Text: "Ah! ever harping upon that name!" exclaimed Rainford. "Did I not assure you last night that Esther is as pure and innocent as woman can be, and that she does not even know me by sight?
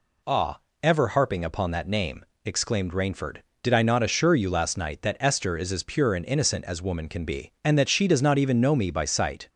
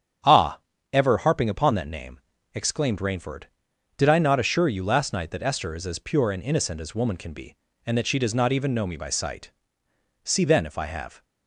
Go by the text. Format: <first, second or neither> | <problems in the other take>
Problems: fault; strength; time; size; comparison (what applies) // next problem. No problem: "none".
first | starts louder than the rest; strong; until 1.5 s; 8.5 dB // goes on to say "See then if I have"; noticeable; from 10.2 s on; 1.0 s long